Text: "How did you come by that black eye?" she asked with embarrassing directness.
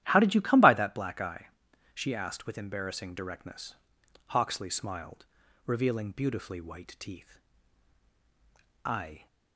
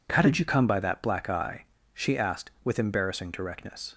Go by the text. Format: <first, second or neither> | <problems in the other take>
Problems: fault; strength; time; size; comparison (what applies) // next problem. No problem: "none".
second | starts louder than the rest; strong; until 1.0 s; 12.5 dB // goes on to say "Hawksley smiled revealing beautifully white teeth I"; strong; from 4.2 s on; 5.0 s long